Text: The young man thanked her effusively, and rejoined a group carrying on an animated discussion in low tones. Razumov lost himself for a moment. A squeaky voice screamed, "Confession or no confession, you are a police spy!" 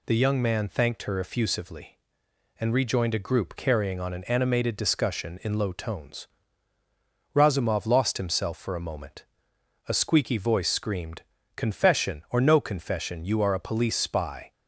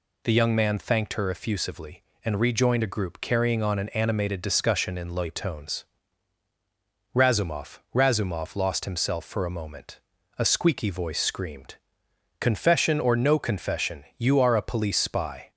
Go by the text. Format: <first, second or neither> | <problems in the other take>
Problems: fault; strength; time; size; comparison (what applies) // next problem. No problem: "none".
first | says "Razumov" twice; at 7.9 s